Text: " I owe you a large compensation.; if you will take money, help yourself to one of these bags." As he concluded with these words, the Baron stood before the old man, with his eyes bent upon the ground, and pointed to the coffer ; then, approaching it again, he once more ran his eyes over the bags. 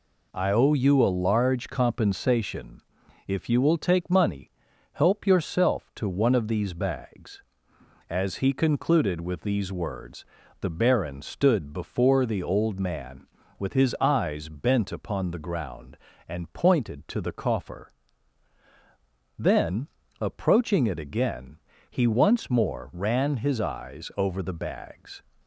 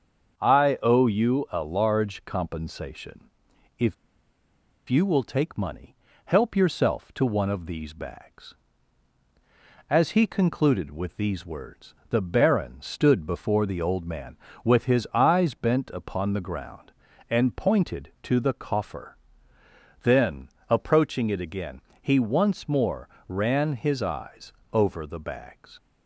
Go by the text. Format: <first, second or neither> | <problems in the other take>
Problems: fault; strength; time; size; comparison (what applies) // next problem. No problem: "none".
first | starts louder than the rest; until 1.4 s; 6.5 dB // pauses between "if" and "you"; noticeable; at 3.9 s; 0.94 s long // pauses between "more" and "ran"; slight; at 23.0 s; 0.18 s long // pauses between "eyes" and "over"; slight; at 24.5 s; 0.18 s long